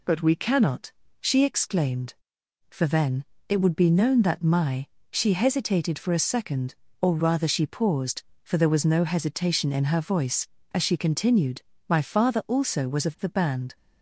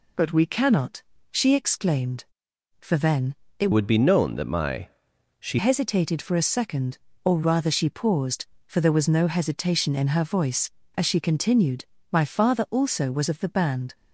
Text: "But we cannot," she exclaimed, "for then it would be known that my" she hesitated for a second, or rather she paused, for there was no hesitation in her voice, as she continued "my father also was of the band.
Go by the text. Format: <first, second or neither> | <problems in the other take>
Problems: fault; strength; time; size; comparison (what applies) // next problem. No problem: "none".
first | pauses between "then" and "it"; slight; at 3.3 s; 0.24 s long; slight in the first // changes voice from "would" to "she"; from 3.7 to 5.5 s; 1.8 s long // pauses between "my" and "she"; noticeable; at 4.8 s; 0.54 s long; slight in the first // pauses between "continued" and "my"; slight; at 11.8 s; 0.26 s long; slight in the first